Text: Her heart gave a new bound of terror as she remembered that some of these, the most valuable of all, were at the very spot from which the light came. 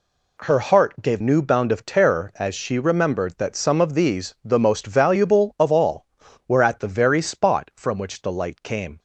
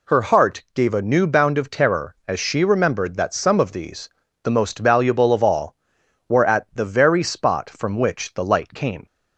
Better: second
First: skips "a"; at 1.2 s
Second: none

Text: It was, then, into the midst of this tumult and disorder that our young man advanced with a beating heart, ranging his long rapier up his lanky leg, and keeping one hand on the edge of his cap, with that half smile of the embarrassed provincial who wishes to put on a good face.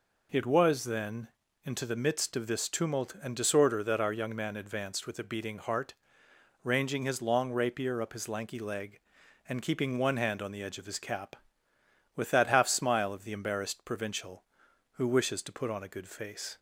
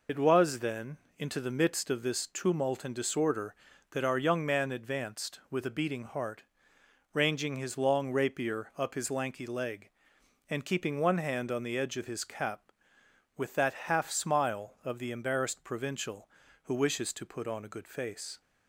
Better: first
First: none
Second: loses the start of "It"; at 0.0 s; 50 ms

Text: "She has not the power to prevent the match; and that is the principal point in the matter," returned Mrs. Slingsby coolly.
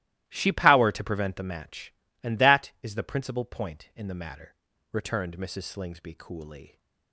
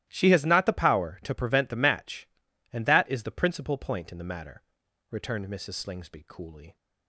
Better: second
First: starts louder than the rest; strong; until 1.2 s; 16.5 dB // skips "has not the"; at 0.4 s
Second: starts louder than the rest; strong; until 1.0 s; 14.5 dB

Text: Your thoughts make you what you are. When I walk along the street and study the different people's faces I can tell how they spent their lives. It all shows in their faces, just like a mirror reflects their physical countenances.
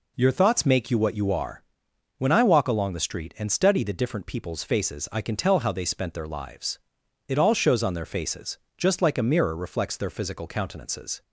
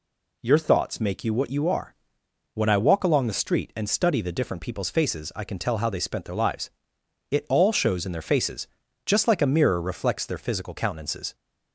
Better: second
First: says "on" for "in"; at 7.8 s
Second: none

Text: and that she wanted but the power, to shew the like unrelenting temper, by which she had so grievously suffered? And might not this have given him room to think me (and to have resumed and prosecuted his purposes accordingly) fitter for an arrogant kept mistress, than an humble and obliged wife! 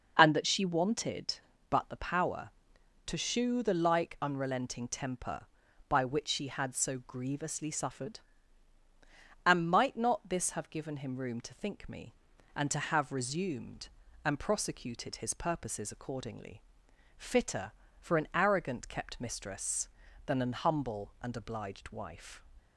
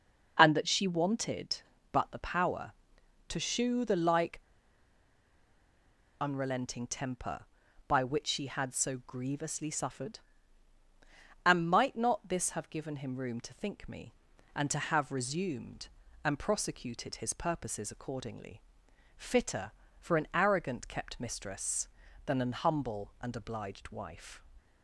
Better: first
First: none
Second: pauses between "like" and "unrelenting"; strong; at 4.3 s; 1.8 s long

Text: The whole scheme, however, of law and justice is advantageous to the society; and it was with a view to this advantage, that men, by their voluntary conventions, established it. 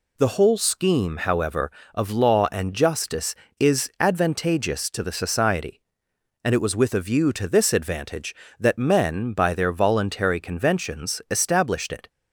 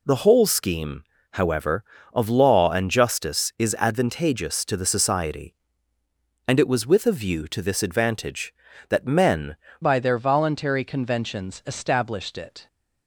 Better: first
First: none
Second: changes voice at "by"; from 9.8 s on; 2.8 s long

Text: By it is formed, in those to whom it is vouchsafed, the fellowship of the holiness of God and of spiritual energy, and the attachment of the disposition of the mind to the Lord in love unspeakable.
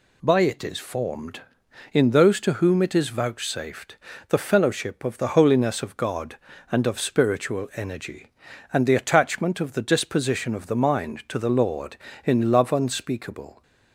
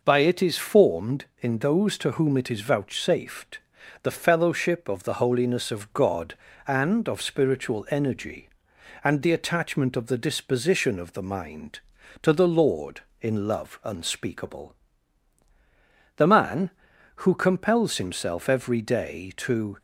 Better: first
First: none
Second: goes on to say "The man who compels himself every day to"; strong; from 16.1 s on; 3.6 s long

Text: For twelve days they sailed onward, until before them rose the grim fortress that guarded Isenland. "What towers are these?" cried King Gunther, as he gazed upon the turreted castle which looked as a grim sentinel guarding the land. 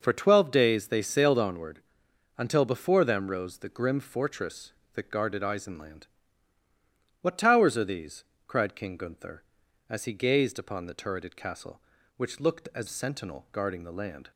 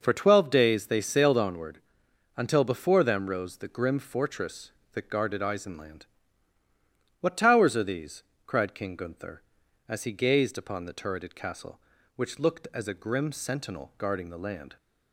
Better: second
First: skips "a grim"; at 12.8 s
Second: none

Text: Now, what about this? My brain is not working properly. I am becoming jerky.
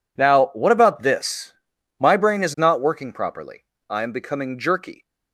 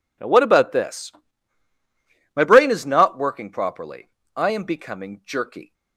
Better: neither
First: none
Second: none

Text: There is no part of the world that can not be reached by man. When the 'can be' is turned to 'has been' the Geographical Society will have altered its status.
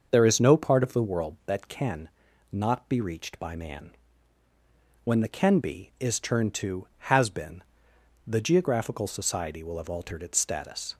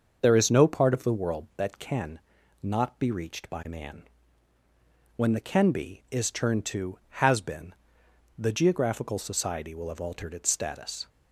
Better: neither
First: starts louder than the rest; until 1.1 s; 6.5 dB // pauses between "can" and "not"; at 2.0 s; 0.42 s long // pauses between "been" and "the"; noticeable; at 7.6 s; 0.64 s long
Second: starts louder than the rest; until 1.2 s; 6.5 dB // pauses between "can" and "not"; at 2.1 s; 0.42 s long // pauses between "been" and "the"; noticeable; at 7.7 s; 0.64 s long

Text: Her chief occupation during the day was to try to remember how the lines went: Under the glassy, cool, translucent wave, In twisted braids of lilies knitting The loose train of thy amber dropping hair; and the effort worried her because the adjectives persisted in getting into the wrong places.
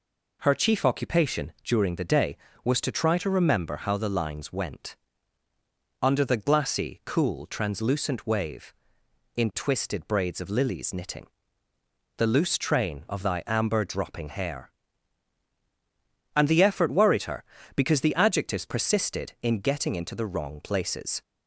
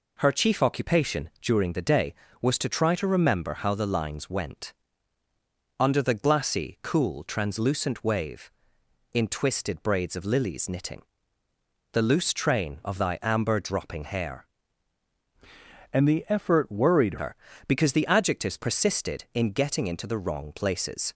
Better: first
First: pauses between "knitting" and "The"; noticeable; at 11.2 s; 0.90 s long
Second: pauses between "knitting" and "The"; noticeable; at 11.0 s; 0.90 s long // changes voice from "and" to "worried"; from 15.9 to 17.1 s; 1.2 s long

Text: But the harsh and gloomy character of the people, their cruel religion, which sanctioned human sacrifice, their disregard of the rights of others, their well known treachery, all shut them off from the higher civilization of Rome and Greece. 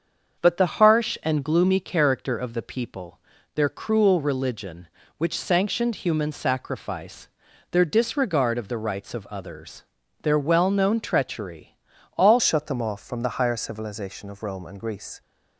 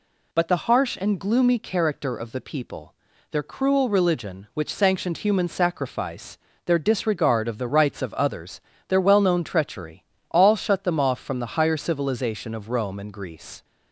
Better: second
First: starts louder than the rest; until 1.4 s; 7 dB // changes voice at "shut"; from 12.3 s on; 2.9 s long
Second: none

